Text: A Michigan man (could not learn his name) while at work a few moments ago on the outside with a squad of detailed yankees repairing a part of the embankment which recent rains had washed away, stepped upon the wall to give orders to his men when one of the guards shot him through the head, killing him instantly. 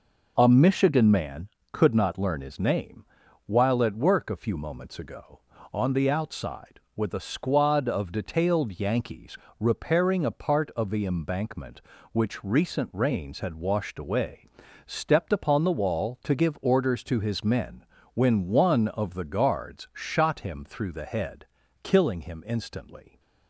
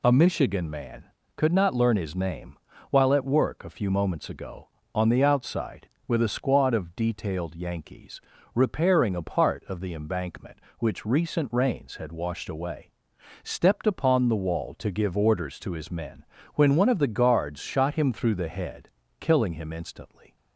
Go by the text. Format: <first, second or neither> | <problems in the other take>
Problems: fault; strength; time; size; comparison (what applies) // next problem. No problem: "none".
neither | pauses between "yankees" and "repairing"; slight; the same in both // pauses between "men" and "when"; slight; the same in both